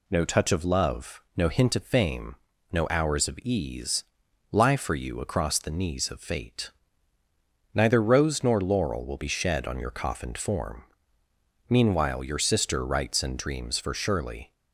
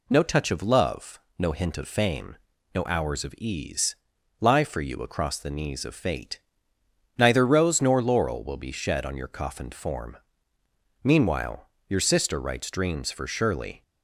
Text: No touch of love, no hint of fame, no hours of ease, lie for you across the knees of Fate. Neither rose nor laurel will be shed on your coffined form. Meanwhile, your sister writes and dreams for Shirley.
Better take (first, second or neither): first